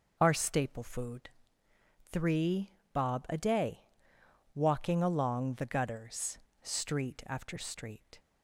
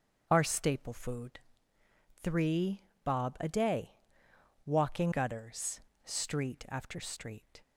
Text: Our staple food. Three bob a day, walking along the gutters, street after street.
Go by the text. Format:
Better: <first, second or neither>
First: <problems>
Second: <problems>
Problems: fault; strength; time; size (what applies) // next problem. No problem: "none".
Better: first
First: pauses between "Three" and "bob"; slight; at 2.7 s; 0.24 s long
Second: starts louder than the rest; until 1.3 s; 7 dB // pauses between "Three" and "bob"; slight; at 2.8 s; 0.24 s long // skips "along the"; at 5.1 s